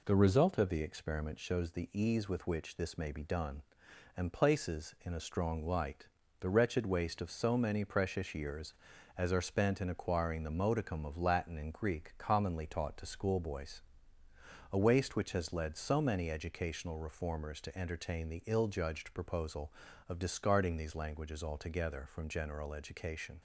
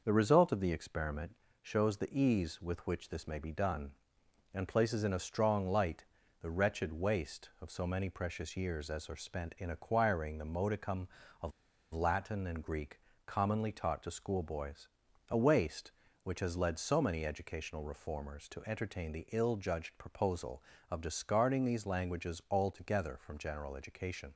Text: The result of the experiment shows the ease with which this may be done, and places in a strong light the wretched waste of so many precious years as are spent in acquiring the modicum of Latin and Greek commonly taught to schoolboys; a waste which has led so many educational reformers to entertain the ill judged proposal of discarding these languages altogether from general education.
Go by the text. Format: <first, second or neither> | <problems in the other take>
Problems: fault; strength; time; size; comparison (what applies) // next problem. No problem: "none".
first | pauses between "experiment" and "shows"; slight; at 1.3 s; 0.26 s long // pauses between "light" and "the"; slight; at 6.0 s; 0.34 s long; slight in the first // pauses between "of" and "Latin"; at 11.5 s; 0.42 s long // pauses between "Greek" and "commonly"; slight; at 13.0 s; 0.24 s long